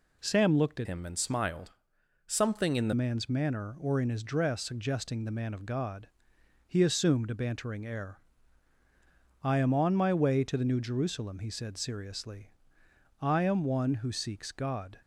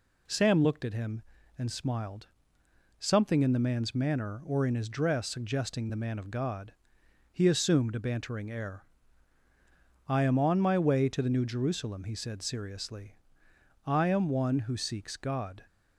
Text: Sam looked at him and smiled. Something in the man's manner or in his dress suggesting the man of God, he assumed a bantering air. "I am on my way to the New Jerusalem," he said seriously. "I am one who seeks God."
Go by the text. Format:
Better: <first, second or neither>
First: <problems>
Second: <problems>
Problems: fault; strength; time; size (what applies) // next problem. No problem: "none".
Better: second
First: changes voice from "him" to "the"; from 0.8 to 2.9 s; 2.1 s long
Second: none